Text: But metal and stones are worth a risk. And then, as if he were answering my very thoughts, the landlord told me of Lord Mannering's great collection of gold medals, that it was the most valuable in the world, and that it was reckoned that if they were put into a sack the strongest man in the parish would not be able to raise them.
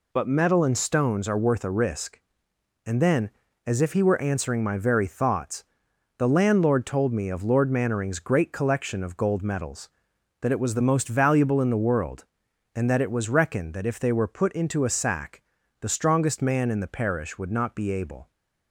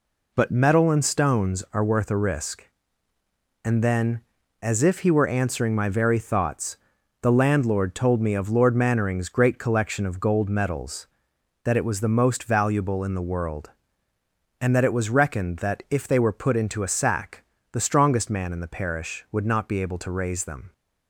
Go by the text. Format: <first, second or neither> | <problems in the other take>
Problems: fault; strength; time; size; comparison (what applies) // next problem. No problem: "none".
second | pauses between "sack" and "the"; at 15.4 s; 0.38 s long; slight in the second // stops before "to raise them"; at 18.3 s